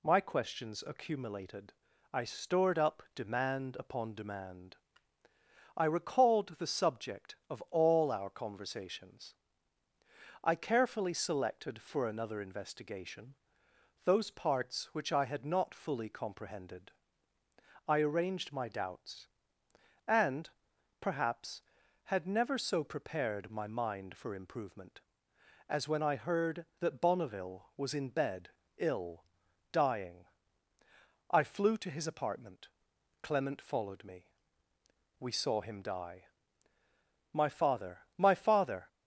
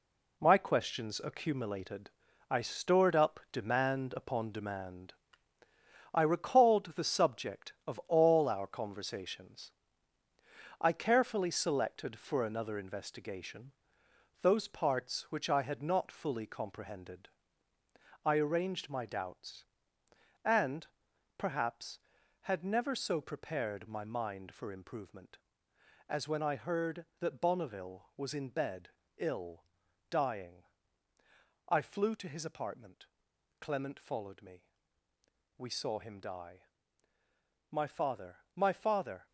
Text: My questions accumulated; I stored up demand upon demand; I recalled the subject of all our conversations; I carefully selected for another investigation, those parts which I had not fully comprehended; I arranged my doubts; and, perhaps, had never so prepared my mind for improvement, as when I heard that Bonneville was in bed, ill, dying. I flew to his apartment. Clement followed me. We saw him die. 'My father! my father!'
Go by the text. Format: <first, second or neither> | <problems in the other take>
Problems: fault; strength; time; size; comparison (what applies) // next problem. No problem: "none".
first | gets quieter; strong; throughout; 8 dB